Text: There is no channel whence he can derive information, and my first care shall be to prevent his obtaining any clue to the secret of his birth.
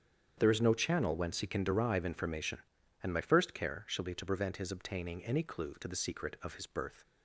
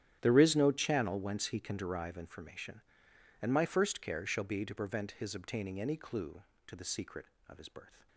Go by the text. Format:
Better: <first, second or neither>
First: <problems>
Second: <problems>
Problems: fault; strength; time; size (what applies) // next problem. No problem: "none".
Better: first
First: starts louder than the rest; strong; until 1.3 s; 8 dB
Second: gets quieter; strong; throughout; 17.5 dB // starts louder than the rest; strong; until 1.2 s; 11 dB